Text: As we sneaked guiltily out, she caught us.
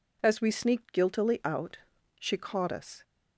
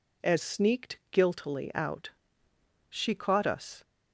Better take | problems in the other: first | skips "we"; at 0.4 s

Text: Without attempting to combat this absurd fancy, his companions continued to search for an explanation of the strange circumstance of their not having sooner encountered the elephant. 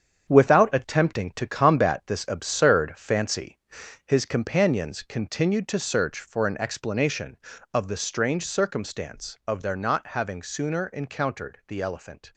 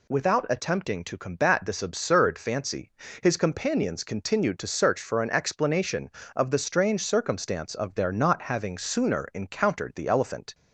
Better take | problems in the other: second | gets quieter; strong; throughout; 8.5 dB

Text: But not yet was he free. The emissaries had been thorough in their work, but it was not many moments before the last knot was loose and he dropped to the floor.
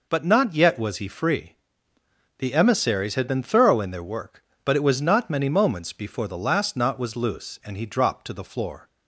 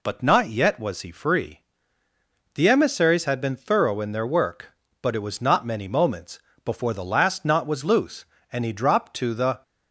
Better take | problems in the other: first | pauses between "moments" and "before"; slight; at 6.3 s; 0.26 s long // stops before "floor"; at 9.6 s

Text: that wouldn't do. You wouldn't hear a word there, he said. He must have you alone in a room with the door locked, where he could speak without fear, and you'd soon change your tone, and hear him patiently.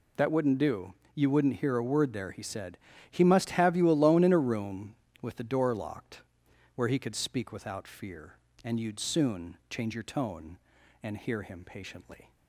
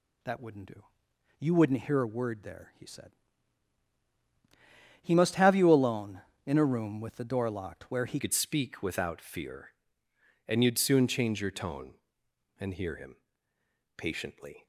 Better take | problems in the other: first | changes voice at "could"; from 8.1 s on; 6.5 s long // pauses between "him" and "patiently"; noticeable; at 13.1 s; 0.80 s long

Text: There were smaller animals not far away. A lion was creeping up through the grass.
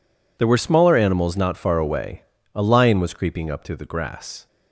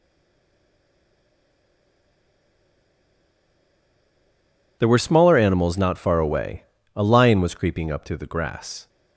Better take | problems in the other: first | stays silent before the first word; strong; until 4.8 s; 4.8 s long

